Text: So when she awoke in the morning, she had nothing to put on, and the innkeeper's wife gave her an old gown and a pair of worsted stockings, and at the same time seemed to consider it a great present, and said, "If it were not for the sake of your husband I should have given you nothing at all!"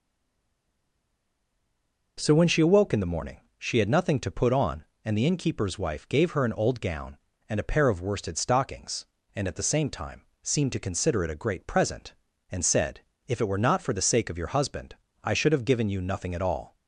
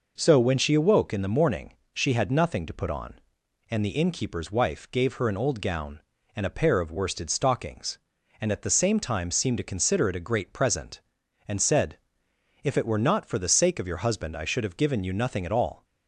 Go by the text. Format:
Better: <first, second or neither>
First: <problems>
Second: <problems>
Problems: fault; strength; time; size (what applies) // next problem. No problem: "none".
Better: second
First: stays silent before the first word; until 2.1 s; 2.1 s long // pauses between "time" and "seemed"; slight; at 10.2 s; 0.18 s long // pauses between "husband" and "I"; slight; at 14.9 s; 0.26 s long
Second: none